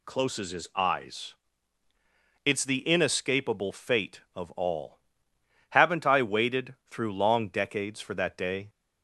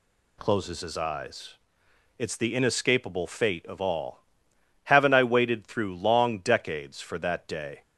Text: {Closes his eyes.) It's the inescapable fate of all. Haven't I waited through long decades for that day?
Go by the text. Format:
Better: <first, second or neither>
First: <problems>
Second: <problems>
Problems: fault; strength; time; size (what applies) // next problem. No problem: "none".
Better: neither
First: none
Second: none